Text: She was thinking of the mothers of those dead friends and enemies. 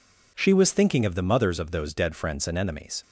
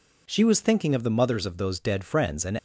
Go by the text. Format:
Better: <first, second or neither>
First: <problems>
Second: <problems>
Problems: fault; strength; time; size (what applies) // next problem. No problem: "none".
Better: first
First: none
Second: stops before "enemies"; at 2.5 s